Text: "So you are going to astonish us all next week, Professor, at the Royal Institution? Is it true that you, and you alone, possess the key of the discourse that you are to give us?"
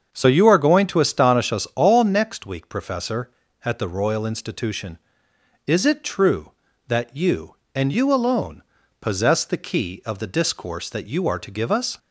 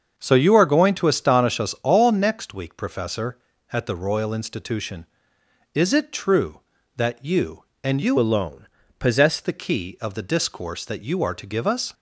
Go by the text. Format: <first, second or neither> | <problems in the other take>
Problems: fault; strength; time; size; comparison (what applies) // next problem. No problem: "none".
first | starts louder than the rest; until 1.1 s; 7 dB; also in the first // changes voice from "alone" to "possess"; from 8.1 to 9.3 s; 1.2 s long